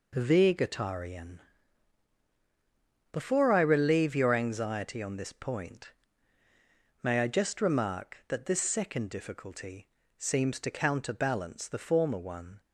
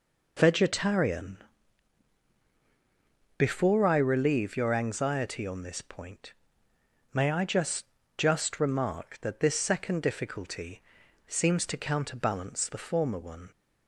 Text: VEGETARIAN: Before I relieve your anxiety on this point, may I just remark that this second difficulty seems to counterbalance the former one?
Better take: first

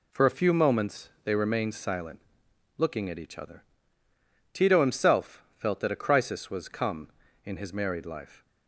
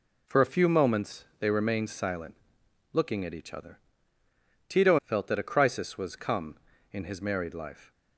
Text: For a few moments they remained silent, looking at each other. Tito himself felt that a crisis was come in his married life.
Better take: first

